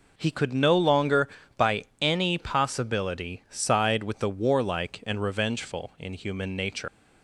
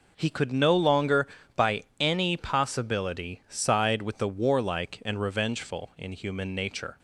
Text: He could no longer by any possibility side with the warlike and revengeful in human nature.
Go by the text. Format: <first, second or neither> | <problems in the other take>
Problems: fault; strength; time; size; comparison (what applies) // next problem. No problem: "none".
second | pauses between "by" and "any"; slight; at 1.8 s; 0.16 s long; slight in the second // leaves "nature" unfinished; at 6.8 s; 115 ms